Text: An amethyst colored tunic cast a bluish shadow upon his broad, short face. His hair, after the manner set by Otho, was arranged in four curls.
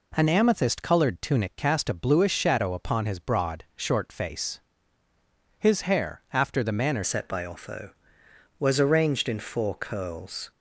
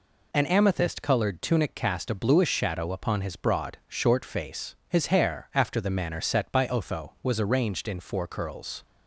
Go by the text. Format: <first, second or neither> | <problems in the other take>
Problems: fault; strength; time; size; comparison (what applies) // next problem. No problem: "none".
second | changes voice at "set"; from 7.0 s on; 3.5 s long